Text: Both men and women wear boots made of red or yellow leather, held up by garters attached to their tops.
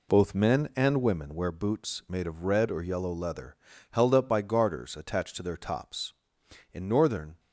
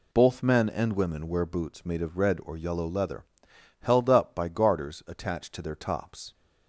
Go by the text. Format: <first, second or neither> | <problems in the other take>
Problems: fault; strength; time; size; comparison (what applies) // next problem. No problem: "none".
second | goes on to say "In northern"; noticeable; from 6.7 s on; 0.66 s long